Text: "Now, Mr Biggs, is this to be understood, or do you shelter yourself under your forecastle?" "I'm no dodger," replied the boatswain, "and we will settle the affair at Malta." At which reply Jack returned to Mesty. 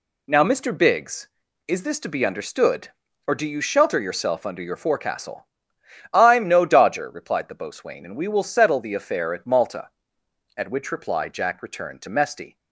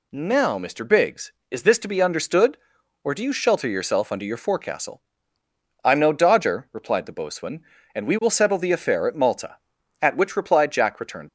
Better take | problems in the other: first | stops before "to Mesty"; at 11.2 s

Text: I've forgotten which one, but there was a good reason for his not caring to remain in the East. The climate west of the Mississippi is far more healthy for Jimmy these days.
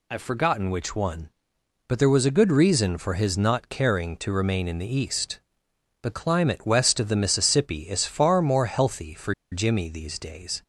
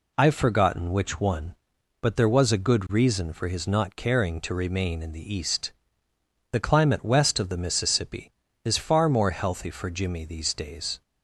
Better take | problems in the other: second | pauses between "for" and "Jimmy"; slight; at 9.3 s; 0.18 s long

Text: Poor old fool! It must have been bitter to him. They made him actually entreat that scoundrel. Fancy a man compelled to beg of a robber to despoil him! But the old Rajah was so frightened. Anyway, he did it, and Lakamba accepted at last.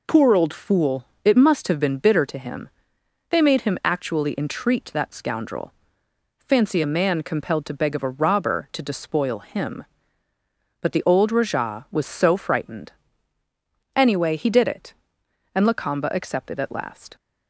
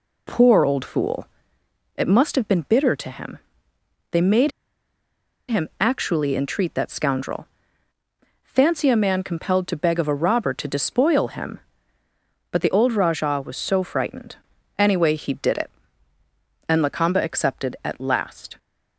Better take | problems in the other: first | pauses between "made" and "him"; at 4.5 s; 0.98 s long

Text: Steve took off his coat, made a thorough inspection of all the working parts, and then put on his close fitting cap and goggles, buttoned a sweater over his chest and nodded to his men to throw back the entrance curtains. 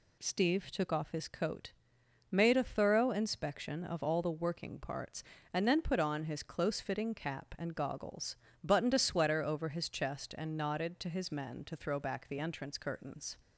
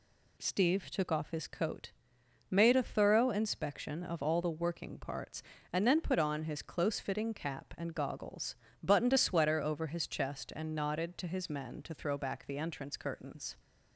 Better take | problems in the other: neither | none

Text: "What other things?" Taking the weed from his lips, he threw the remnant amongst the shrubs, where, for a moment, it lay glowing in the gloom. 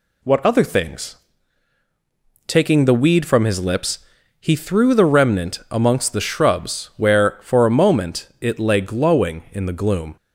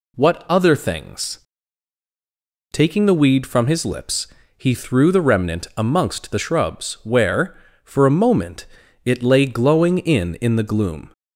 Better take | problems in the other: first | says "in" twice; at 10.3 s

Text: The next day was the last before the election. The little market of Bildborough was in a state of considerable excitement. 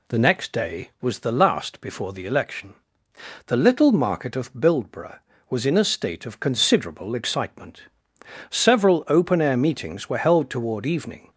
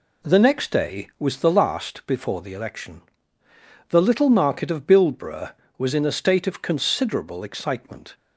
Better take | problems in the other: second | goes on to say "Several open air meetings were held toward evening"; strong; from 8.4 s on; 2.8 s long

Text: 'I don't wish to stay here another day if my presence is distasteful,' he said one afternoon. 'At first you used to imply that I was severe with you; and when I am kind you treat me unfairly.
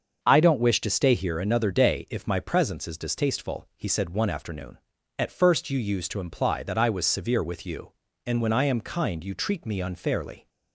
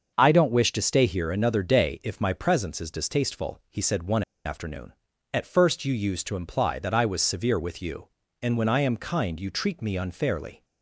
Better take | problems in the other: first | starts louder than the rest; until 1.1 s; 6.5 dB; also in the first // pauses between "one" and "afternoon"; slight; at 4.2 s; 0.24 s long

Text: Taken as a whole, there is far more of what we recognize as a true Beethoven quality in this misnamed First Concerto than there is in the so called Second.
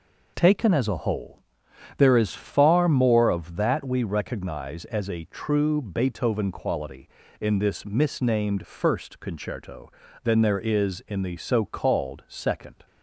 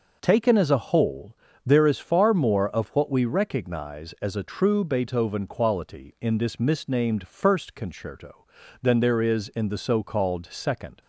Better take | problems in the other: second | says "that" for "what"; at 3.5 s

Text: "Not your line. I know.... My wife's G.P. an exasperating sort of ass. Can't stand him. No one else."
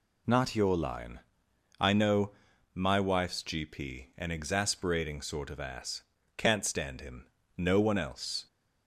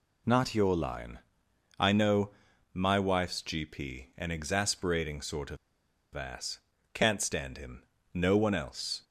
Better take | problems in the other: first | pauses between "of" and "ass"; noticeable; at 5.5 s; 0.58 s long

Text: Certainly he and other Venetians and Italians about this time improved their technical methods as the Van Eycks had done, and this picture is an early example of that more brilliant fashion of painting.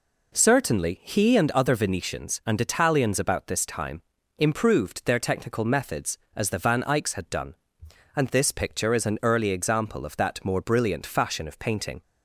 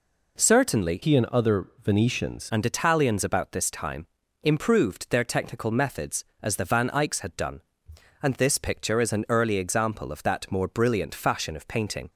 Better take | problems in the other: first | changes voice from "he" to "Venetians"; from 1.0 to 2.5 s; 1.5 s long // pauses between "time" and "improved"; at 4.0 s; 0.38 s long; also in the first

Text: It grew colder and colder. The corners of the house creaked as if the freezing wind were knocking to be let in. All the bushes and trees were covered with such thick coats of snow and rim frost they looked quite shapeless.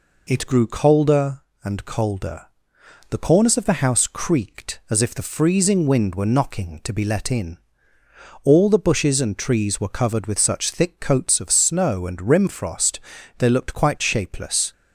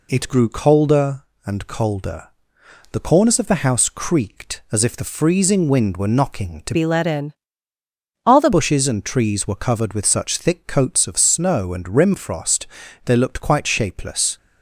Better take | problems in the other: first | changes voice from "be" to "the"; from 6.7 to 8.5 s; 1.8 s long // pauses between "frost" and "they"; at 12.6 s; 0.38 s long; also in the first

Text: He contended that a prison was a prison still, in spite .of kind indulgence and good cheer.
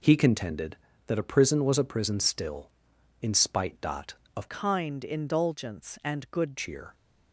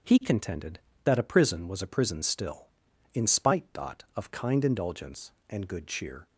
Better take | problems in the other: second | changes voice from "kind" to "good"; from 4.4 to 6.5 s; 2.1 s long

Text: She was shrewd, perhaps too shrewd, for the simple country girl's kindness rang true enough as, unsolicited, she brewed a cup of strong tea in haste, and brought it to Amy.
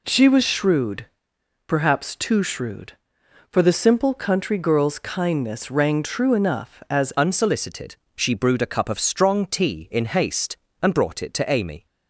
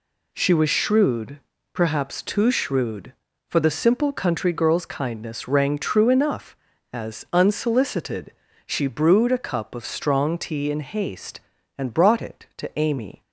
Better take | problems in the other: second | changes voice at "unsolicited"; from 7.1 s on; 4.7 s long

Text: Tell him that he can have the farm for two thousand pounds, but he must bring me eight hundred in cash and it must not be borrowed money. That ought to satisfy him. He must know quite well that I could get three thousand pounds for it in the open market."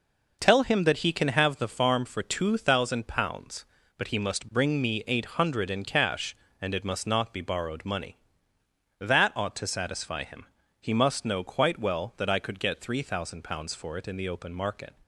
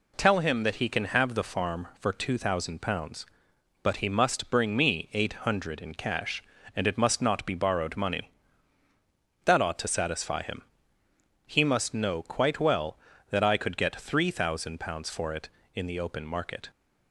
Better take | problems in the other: neither | none

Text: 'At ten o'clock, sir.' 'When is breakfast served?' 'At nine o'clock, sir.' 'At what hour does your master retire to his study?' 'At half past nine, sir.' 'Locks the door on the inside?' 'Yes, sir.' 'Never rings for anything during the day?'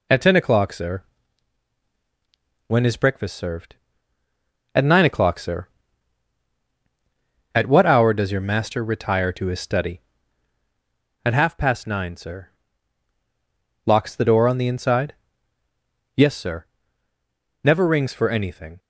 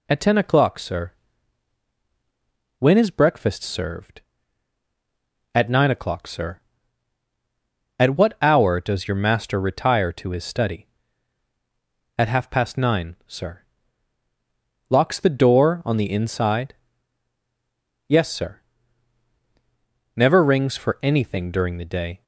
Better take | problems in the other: second | stops before "during the day"; at 18.7 s

